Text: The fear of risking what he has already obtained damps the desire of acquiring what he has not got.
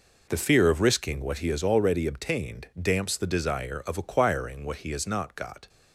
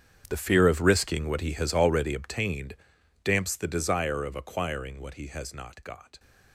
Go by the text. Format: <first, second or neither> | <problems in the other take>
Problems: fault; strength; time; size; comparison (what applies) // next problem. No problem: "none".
first | gets quieter; strong; throughout; 17.5 dB // pauses between "obtained" and "damps"; noticeable; at 2.7 s; 0.48 s long